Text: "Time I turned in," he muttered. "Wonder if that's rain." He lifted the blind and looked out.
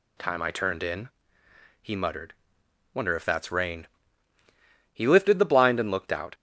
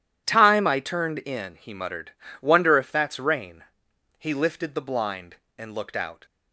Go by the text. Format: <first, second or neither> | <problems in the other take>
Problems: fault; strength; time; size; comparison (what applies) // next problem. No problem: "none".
neither | none